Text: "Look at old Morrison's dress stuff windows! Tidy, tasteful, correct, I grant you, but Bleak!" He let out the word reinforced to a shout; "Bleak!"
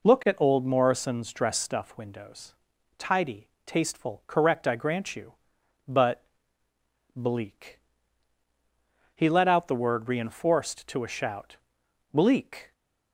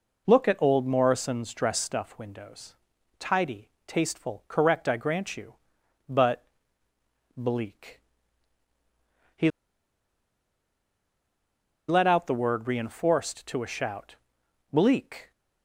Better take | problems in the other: first | pauses between "but" and "Bleak"; noticeable; at 6.4 s; 0.90 s long; noticeable in the first // pauses between "He" and "let"; strong; at 9.4 s; 2.3 s long

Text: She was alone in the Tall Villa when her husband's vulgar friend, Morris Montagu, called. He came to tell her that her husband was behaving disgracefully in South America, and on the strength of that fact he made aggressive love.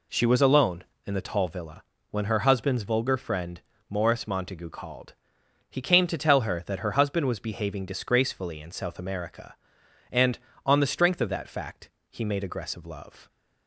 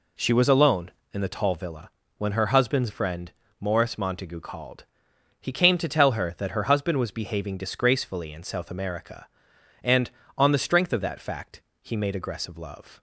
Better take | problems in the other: first | pauses between "Villa" and "when"; slight; at 1.9 s; 0.26 s long; slight in the first // skips "vulgar"; at 2.8 s // pauses between "fact" and "he"; slight; at 11.6 s; 0.18 s long; slight in the first

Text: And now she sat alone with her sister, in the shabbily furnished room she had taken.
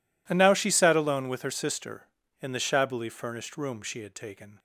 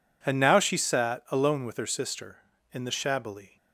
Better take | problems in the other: first | stops before "furnished room she had taken"; at 3.5 s

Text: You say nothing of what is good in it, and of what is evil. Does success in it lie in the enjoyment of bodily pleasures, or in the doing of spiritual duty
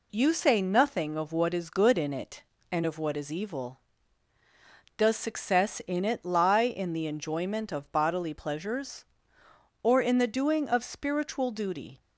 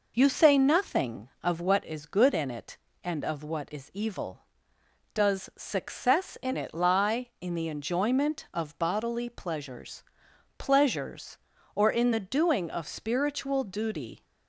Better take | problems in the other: first | says "pleasures" twice; at 10.5 s

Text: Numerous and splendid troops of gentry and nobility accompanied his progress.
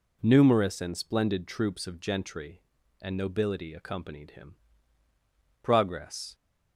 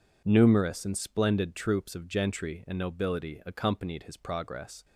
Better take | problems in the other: second | says "him" for "his"; at 4.3 s

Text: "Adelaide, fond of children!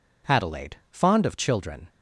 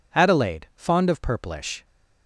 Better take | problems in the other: first | says "purplish" for "children"; at 1.2 s

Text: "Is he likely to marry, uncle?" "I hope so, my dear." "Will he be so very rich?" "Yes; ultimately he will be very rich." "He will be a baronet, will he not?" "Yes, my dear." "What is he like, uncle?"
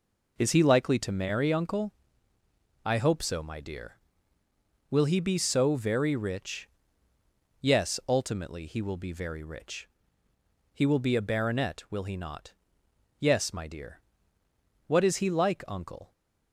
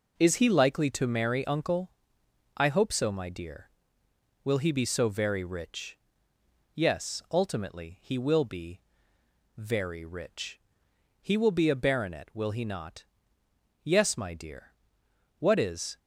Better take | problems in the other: first | pauses between "be" and "very"; noticeable; at 8.7 s; 0.78 s long // stops before "he like uncle"; at 15.9 s

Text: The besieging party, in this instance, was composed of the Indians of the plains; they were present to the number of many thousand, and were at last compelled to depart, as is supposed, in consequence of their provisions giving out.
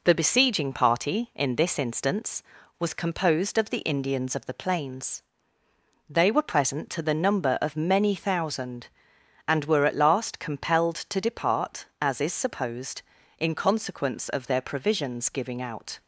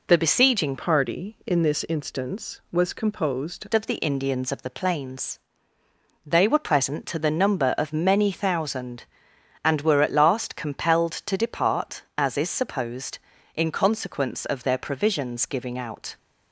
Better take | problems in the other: first | changes voice from "party" to "composed"; from 0.7 to 3.6 s; 2.9 s long

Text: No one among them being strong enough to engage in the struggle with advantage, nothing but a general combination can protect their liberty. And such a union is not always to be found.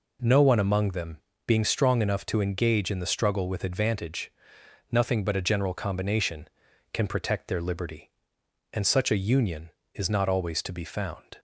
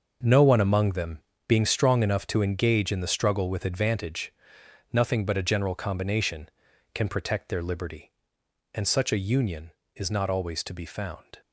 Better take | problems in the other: first | gets quieter; strong; throughout; 11.5 dB // pauses between "them" and "being"; slight; at 1.1 s; 0.30 s long; slight in the first

